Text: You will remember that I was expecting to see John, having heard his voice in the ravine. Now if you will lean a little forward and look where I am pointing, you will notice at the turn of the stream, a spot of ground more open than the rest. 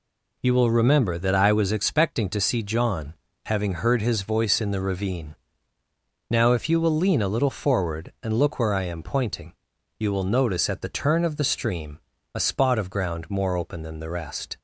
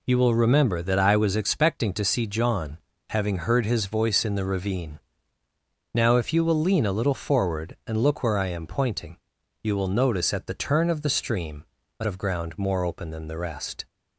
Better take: first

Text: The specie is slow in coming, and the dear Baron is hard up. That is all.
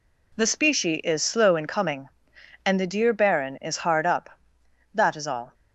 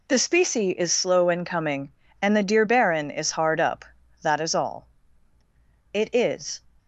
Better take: first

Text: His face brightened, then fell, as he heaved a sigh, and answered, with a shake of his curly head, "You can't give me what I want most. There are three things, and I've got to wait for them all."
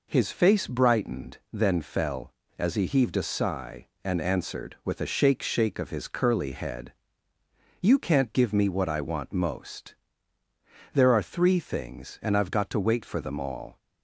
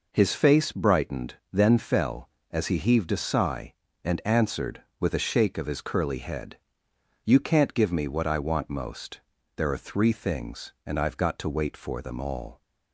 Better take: second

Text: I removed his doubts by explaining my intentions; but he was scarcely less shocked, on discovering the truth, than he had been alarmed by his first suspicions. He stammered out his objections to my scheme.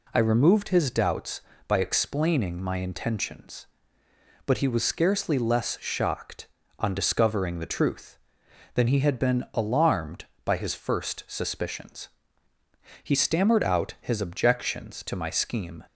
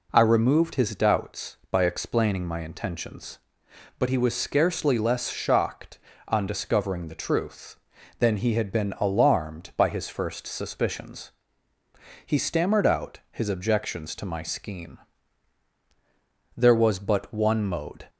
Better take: first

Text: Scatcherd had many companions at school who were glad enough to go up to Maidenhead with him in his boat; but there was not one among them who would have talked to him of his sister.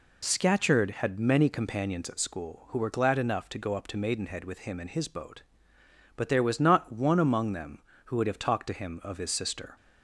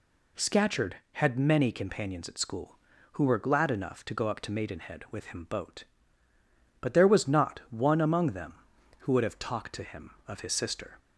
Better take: first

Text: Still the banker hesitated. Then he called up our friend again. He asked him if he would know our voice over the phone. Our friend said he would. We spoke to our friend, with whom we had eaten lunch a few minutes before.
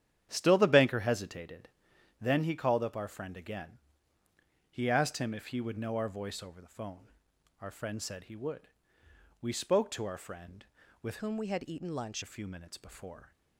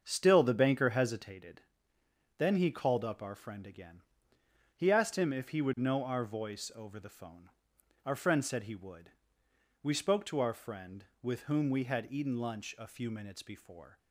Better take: second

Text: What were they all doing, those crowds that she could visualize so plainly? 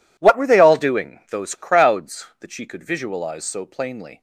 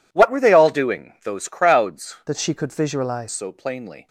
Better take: first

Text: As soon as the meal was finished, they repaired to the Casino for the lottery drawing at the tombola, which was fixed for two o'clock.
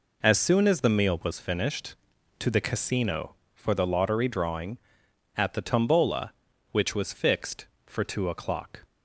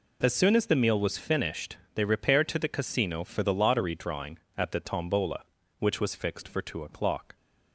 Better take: second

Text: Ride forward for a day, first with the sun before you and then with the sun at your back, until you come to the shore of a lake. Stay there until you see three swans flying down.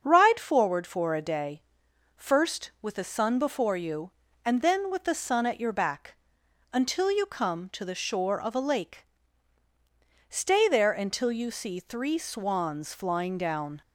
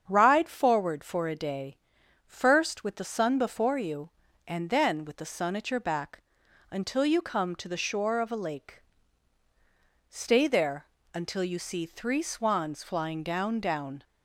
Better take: first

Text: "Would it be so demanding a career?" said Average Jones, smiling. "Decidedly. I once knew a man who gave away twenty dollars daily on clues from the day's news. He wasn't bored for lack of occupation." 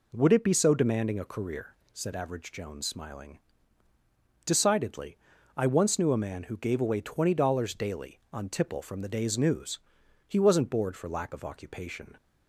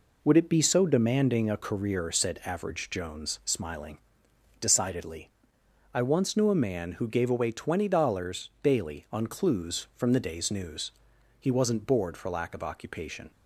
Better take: second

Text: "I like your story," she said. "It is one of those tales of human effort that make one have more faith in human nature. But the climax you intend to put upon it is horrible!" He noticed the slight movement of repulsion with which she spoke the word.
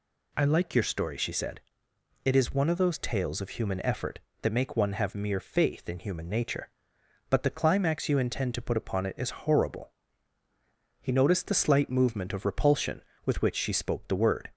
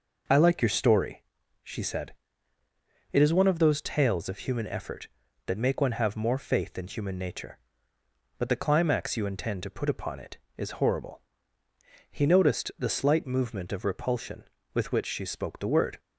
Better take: second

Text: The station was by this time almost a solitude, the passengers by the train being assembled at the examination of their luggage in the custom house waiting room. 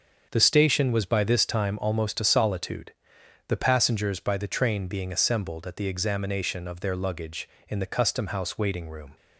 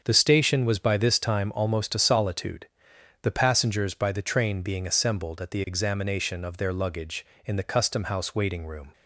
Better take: neither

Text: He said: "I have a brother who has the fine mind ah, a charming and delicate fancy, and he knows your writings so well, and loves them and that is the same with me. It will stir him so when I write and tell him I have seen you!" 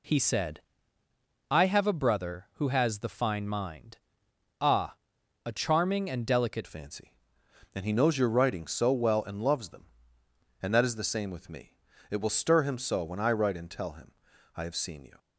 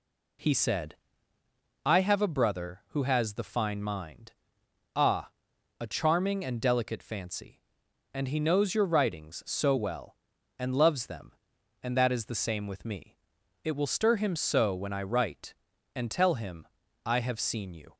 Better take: second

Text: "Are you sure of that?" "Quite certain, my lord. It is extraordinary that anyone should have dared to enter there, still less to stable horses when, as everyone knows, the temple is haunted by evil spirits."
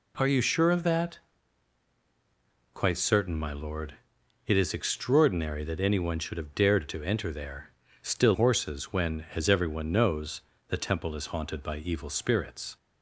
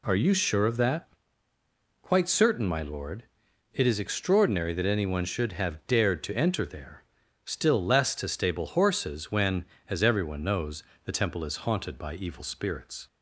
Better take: second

